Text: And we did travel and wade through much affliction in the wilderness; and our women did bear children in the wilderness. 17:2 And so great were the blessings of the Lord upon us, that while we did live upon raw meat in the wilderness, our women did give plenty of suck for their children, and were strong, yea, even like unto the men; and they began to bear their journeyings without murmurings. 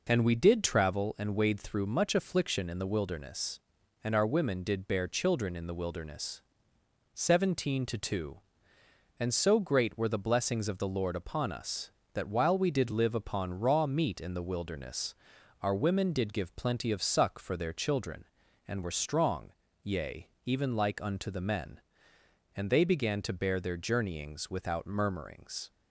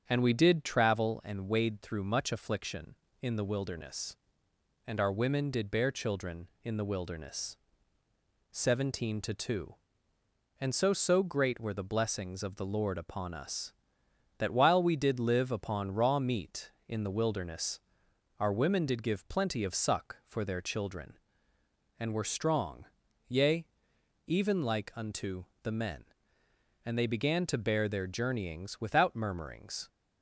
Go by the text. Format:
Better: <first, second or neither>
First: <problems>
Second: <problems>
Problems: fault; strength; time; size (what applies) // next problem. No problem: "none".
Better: first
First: none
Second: starts louder than the rest; strong; until 1.0 s; 7.5 dB // says "so" twice; at 10.9 s // pauses between "unto" and "the"; slight; at 25.4 s; 0.18 s long